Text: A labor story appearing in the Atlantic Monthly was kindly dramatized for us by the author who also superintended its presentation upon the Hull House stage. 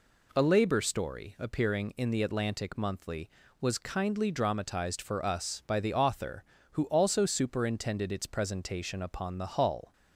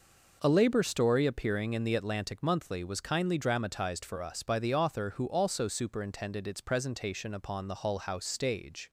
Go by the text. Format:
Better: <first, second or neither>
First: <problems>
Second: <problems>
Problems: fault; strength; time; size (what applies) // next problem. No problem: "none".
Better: second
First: stops before "House stage"; at 9.9 s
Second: none